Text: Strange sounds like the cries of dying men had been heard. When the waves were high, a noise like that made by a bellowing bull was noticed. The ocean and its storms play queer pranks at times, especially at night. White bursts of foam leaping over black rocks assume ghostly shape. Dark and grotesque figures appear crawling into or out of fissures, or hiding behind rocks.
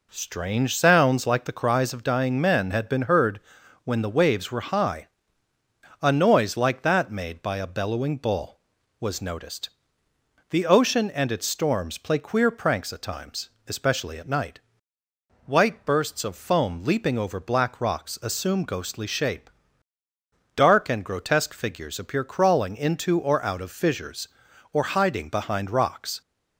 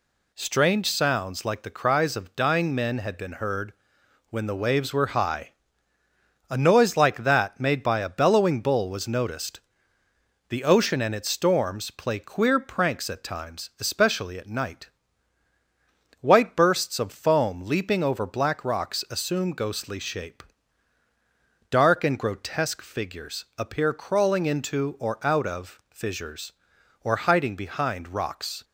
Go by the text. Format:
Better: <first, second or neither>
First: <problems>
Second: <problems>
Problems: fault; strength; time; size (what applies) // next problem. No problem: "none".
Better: neither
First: none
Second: none